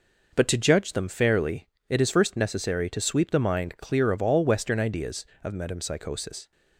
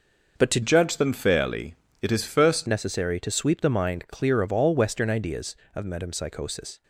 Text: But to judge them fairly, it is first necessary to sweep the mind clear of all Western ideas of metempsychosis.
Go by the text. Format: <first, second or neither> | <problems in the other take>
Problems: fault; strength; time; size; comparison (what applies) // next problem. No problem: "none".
first | starts louder than the rest; noticeable; until 1.4 s; 6 dB // changes voice from "judge" to "first"; from 0.6 to 2.6 s; 2.0 s long